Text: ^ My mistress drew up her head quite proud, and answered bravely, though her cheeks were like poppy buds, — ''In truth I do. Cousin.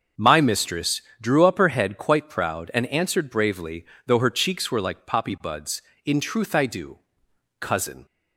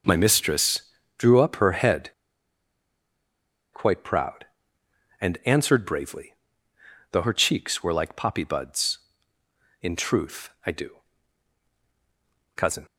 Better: first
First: starts louder than the rest; until 1.3 s; 6.5 dB // pauses between "mistress" and "drew"; slight; at 1.0 s; 0.20 s long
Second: starts louder than the rest; noticeable; until 1.4 s; 6 dB // pauses between "mistress" and "drew"; slight; at 0.8 s; 0.36 s long // pauses between "head" and "quite"; strong; at 2.1 s; 1.6 s long // pauses between "truth" and "I"; slight; at 10.5 s; 0.16 s long

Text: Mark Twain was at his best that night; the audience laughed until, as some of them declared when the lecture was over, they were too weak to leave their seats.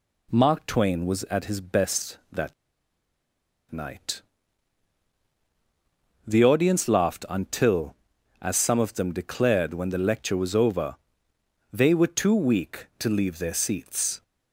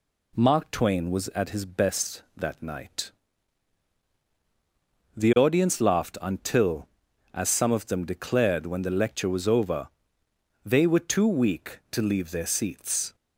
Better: second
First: pauses between "that" and "night"; at 2.5 s; 1.1 s long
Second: none

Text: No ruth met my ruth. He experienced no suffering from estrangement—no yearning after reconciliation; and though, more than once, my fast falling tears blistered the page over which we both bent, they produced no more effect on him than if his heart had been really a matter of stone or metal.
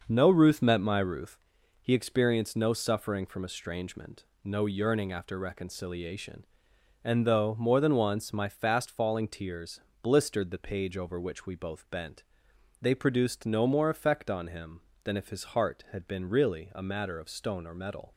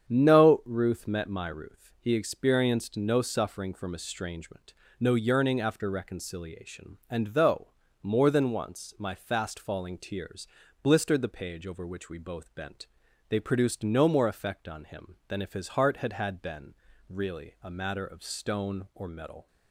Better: first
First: starts louder than the rest; noticeable; until 1.0 s; 6 dB // pauses between "tears" and "blistered"; slight; at 9.7 s; 0.24 s long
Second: starts louder than the rest; strong; until 1.1 s; 8 dB // pauses between "tears" and "blistered"; slight; at 10.4 s; 0.36 s long // says "had" twice; at 16.1 s // pauses between "been" and "really"; slight; at 16.7 s; 0.34 s long

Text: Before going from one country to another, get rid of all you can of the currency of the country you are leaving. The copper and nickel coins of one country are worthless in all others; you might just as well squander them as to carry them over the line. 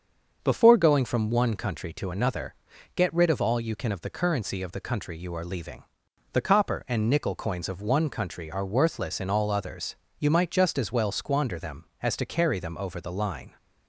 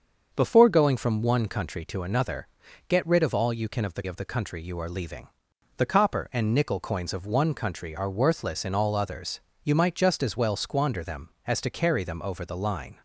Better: first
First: starts louder than the rest; until 1.4 s; 6.5 dB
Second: starts louder than the rest; until 1.3 s; 6.5 dB // skips "currency"; at 4.0 s

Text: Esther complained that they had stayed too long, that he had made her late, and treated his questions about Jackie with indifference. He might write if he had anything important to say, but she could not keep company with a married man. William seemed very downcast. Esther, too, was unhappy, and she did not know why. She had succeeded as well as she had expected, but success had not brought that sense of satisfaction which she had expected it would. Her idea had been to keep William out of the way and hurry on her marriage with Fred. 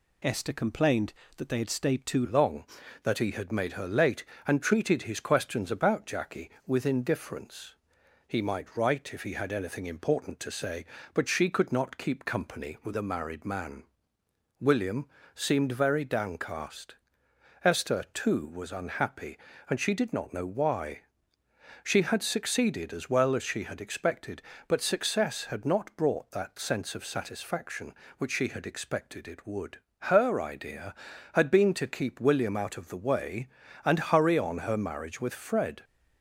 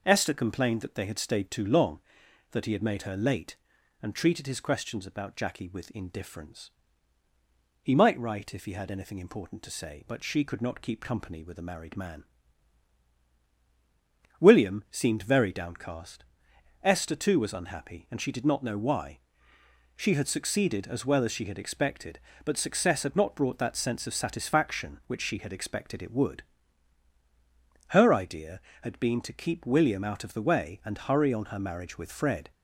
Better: second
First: changes voice at "long"; from 2.2 s on; 33.6 s long // pauses between "William" and "seemed"; slight; at 15.0 s; 0.26 s long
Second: none

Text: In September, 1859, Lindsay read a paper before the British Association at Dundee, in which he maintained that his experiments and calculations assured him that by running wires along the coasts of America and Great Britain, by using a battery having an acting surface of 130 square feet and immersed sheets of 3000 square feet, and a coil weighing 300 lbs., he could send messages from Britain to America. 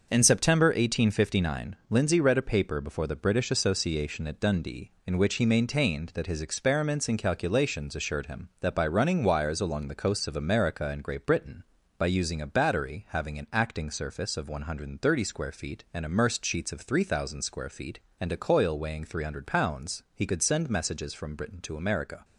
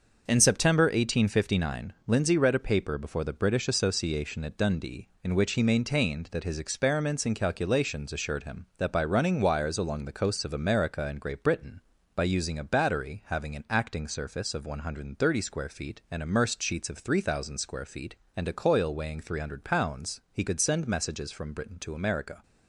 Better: neither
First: starts louder than the rest; until 1.1 s; 6 dB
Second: starts louder than the rest; until 1.3 s; 6 dB

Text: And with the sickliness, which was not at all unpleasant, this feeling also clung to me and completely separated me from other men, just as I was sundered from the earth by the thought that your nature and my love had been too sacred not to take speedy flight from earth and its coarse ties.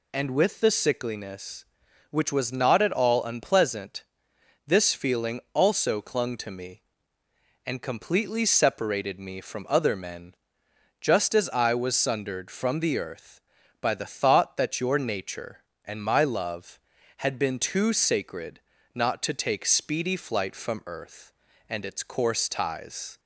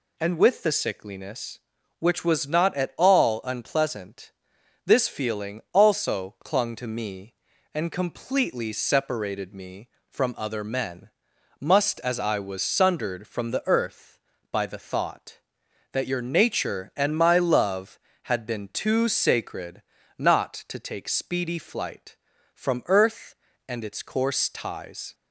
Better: first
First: pauses between "sacred" and "not"; slight; at 18.5 s; 0.36 s long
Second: says "must" for "just"; at 11.5 s // pauses between "sacred" and "not"; slight; at 19.8 s; 0.36 s long

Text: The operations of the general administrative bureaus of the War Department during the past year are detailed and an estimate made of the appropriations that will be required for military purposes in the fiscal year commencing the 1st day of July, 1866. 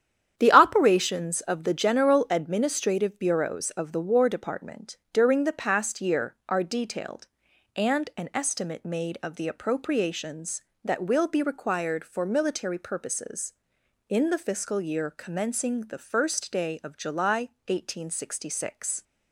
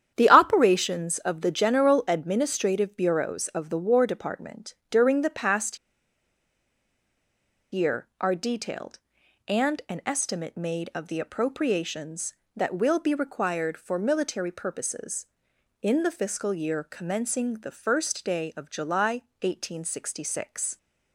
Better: first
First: starts louder than the rest; strong; until 1.3 s; 9.5 dB // pauses between "Department" and "during"; slight; at 4.9 s; 0.16 s long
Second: starts louder than the rest; strong; until 1.1 s; 9.5 dB // pauses between "Department" and "during"; slight; at 4.7 s; 0.16 s long // pauses between "past" and "year"; strong; at 5.7 s; 1.9 s long

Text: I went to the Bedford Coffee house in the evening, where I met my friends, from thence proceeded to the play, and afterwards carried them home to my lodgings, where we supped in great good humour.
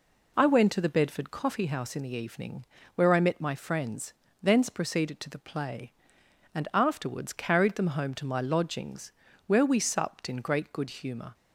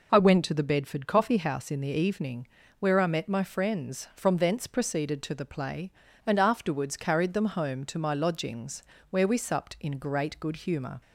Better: second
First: skips "from"; at 4.2 s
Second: none

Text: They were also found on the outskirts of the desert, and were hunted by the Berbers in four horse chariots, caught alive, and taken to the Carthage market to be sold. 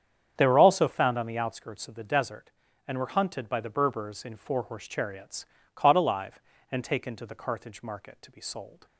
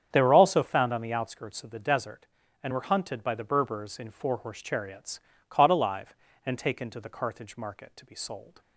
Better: neither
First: starts louder than the rest; strong; until 1.3 s; 8 dB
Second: starts louder than the rest; strong; until 1.1 s; 8 dB

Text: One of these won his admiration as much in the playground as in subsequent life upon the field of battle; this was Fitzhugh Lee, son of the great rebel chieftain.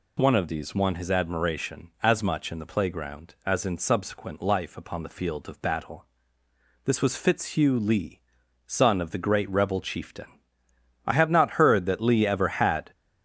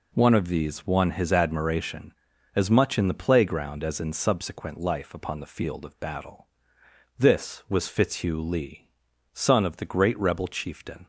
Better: second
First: goes on to say "I have not heard that Lee ever had"; strong; from 11.0 s on; 1.8 s long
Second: none

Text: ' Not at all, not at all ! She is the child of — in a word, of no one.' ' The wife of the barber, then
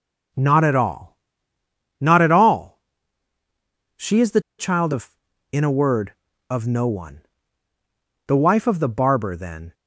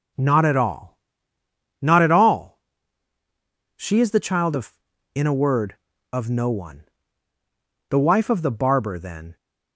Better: second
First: pauses between "the" and "child"; slight; at 4.4 s; 0.17 s long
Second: none

